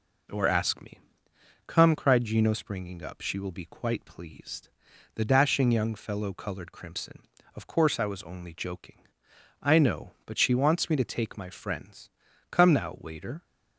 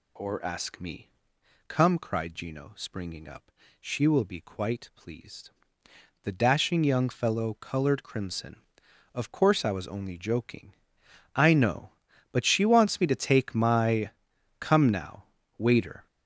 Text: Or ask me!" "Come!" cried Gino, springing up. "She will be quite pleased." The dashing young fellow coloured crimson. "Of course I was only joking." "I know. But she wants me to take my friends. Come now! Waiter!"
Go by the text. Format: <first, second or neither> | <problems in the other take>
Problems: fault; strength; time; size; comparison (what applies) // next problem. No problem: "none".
first | skips "friends"; at 14.3 s